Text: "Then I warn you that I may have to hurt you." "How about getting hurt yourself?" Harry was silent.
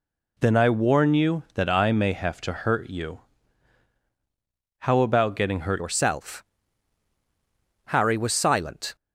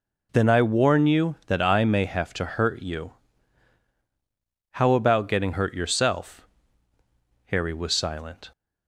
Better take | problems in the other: second | changes voice at "yourself"; from 5.7 s on; 3.2 s long

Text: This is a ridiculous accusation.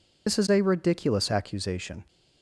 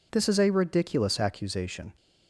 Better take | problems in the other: second | loses the start of "This"; at 0.2 s; 60 ms

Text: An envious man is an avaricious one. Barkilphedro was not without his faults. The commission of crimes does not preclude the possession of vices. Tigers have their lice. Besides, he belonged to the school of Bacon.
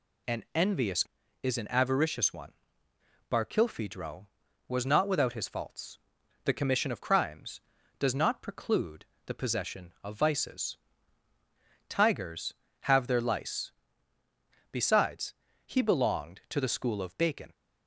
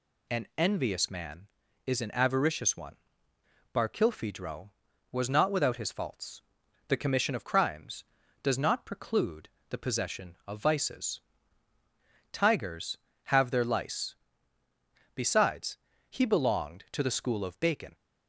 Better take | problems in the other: second | skips "man"; at 1.2 s // pauses between "preclude" and "the"; slight; at 9.0 s; 0.20 s long; slight in the second

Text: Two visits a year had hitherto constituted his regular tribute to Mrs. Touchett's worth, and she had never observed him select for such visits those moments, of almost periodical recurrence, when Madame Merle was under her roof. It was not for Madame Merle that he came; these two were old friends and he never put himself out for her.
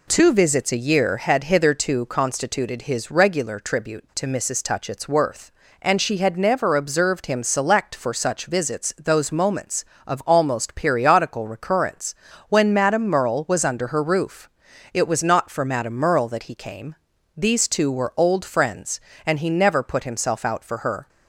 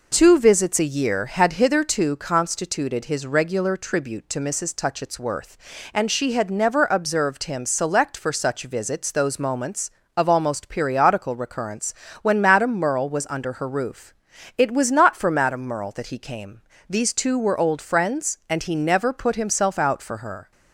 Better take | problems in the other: neither | none

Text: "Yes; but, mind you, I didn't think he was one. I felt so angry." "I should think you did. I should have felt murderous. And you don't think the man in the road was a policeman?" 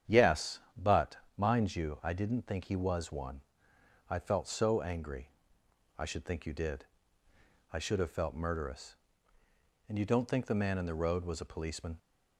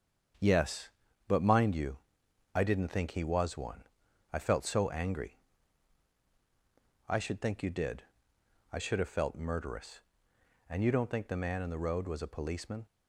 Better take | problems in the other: neither | starts louder than the rest; strong; the same in both

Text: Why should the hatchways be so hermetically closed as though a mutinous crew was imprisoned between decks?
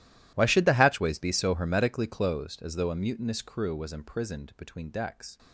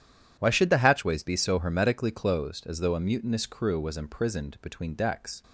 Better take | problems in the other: second | gets quieter; strong; throughout; 20 dB

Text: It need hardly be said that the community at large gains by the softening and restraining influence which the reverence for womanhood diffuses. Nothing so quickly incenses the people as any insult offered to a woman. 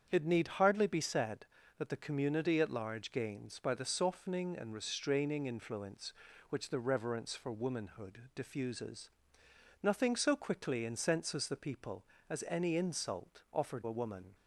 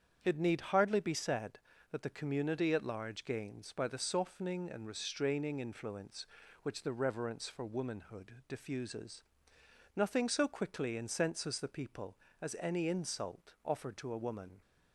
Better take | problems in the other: second | starts louder than the rest; strong; until 1.1 s; 7.5 dB; strong in the second // skips "to"; at 13.8 s

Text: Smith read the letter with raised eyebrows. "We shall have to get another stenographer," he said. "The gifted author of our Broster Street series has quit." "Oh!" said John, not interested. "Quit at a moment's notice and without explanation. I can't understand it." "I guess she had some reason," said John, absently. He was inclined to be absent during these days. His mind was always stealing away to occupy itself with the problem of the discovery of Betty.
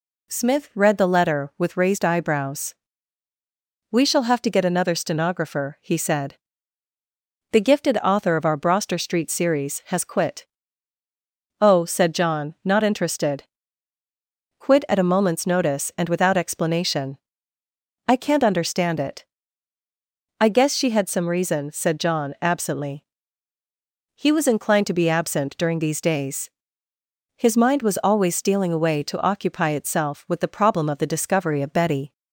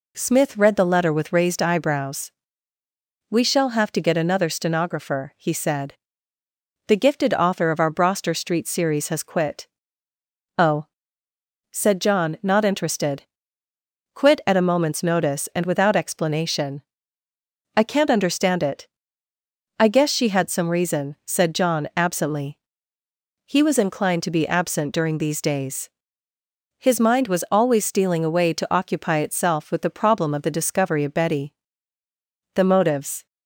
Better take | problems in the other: first | goes on to say "The motives"; noticeable; from 32.5 s on; 0.72 s long

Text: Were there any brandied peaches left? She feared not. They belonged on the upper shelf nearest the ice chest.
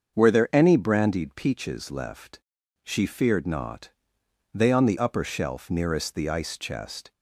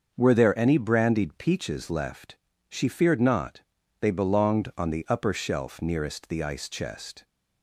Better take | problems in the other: second | starts louder than the rest; until 1.2 s; 6.5 dB; also in the second // skips "belonged"; at 4.7 s

